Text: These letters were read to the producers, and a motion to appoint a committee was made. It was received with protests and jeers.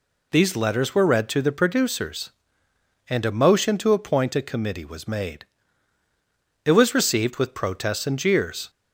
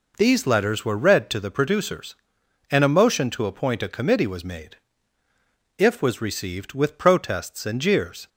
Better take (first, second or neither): first